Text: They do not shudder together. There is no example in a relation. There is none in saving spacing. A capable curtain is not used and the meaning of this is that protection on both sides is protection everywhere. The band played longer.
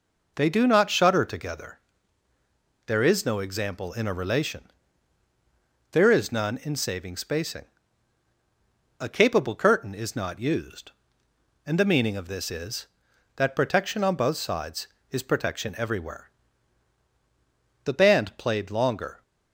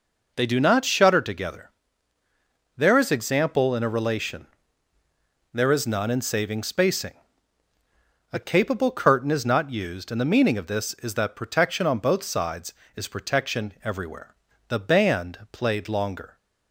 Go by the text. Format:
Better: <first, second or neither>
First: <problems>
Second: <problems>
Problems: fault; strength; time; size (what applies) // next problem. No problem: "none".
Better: first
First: none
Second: skips "no"; at 3.1 s